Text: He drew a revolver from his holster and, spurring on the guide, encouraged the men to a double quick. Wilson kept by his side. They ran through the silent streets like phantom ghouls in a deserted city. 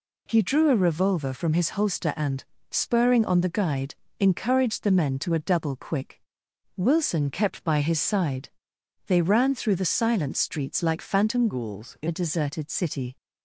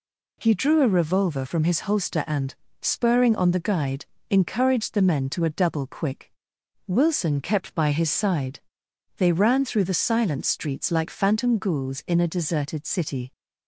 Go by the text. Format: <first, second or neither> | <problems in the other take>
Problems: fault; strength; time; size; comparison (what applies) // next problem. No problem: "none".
second | changes voice from "ghouls" to "in"; from 11.4 to 12.0 s; 0.6 s long